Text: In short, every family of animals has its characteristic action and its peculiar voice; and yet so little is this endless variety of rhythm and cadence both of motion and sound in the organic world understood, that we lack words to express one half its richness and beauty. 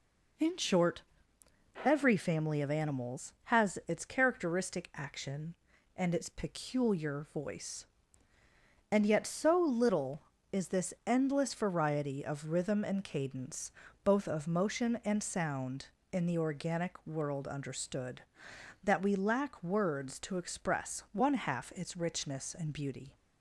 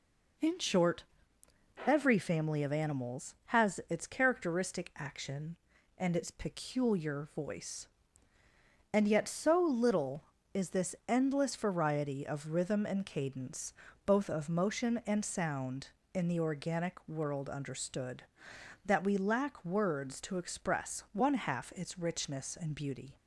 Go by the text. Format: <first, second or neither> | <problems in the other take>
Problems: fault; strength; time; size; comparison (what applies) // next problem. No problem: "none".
neither | pauses between "cadence" and "both"; slight; the same in both